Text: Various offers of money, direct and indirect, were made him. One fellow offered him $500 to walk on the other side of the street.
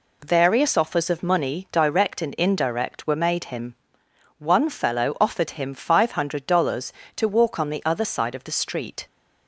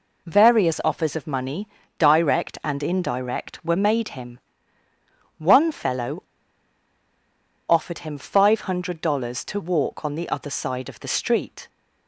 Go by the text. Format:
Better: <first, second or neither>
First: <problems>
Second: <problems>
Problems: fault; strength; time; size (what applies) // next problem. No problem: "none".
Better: first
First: none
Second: pauses between "fellow" and "offered"; strong; at 6.2 s; 1.4 s long